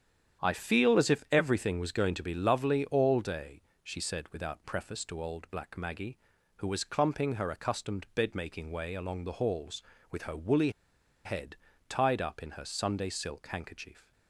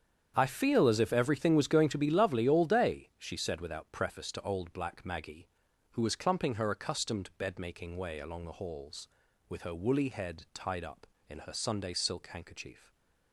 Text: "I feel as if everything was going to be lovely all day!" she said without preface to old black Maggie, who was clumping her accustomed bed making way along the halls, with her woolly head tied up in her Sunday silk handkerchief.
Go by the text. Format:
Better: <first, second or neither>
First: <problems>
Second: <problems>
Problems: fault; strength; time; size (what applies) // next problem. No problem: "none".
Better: second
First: starts louder than the rest; strong; until 1.4 s; 9 dB // pauses between "woolly" and "head"; noticeable; at 10.7 s; 0.54 s long // pauses between "head" and "tied"; slight; at 11.5 s; 0.32 s long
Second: starts louder than the rest; strong; until 1.3 s; 8 dB